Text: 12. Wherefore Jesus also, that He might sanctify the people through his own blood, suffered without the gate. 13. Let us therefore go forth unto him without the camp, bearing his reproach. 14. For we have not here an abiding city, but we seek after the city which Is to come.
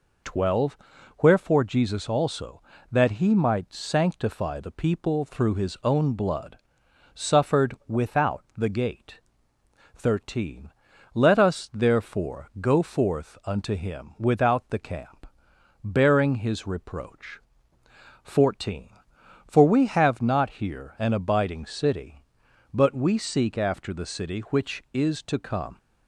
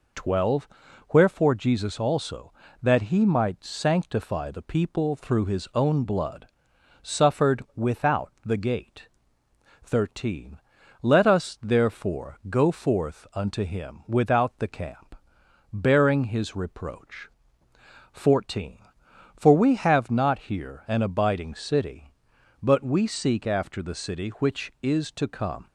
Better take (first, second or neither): neither